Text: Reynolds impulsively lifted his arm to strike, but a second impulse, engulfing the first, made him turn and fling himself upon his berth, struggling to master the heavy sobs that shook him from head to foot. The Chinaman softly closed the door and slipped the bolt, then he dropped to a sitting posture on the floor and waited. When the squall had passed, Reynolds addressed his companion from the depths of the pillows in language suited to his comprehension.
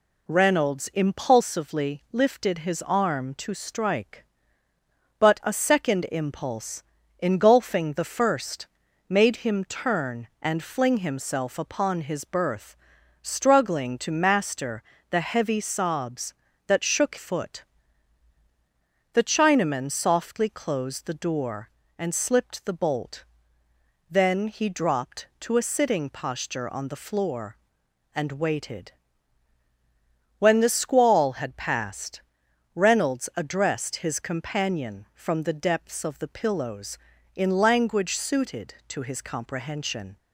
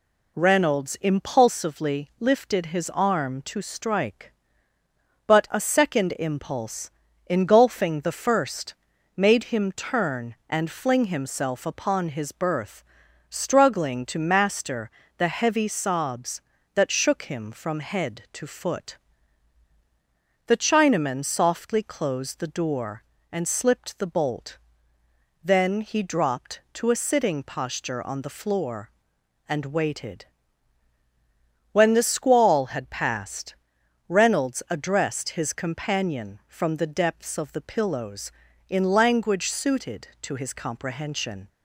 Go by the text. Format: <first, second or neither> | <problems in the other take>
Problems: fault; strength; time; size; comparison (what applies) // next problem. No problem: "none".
second | pauses between "master" and "the"; slight; at 14.8 s; 0.28 s long; slight in the second // skips "him from head to"; at 17.1 s